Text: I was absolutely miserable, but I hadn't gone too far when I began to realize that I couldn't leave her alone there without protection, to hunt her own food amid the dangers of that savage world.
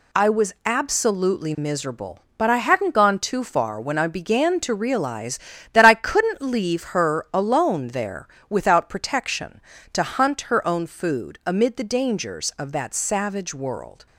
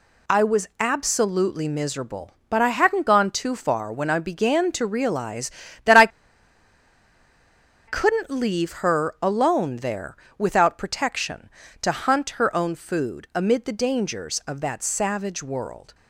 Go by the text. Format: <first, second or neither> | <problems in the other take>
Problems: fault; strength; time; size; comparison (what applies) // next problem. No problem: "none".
first | pauses between "I" and "couldn't"; strong; at 6.0 s; 1.7 s long // pauses between "there" and "without"; slight; at 10.1 s; 0.20 s long; slight in the first